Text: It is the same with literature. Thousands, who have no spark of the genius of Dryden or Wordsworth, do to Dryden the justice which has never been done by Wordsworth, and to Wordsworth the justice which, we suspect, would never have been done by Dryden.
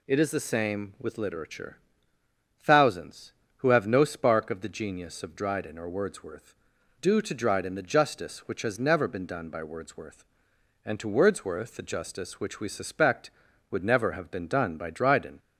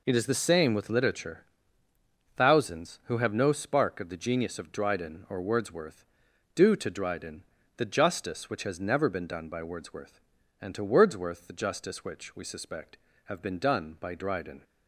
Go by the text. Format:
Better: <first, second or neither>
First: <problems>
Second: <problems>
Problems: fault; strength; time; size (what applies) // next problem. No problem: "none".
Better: first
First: none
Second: pauses between "Dryden" and "the"; slight; at 7.4 s; 0.34 s long // skips "would never"; at 13.1 s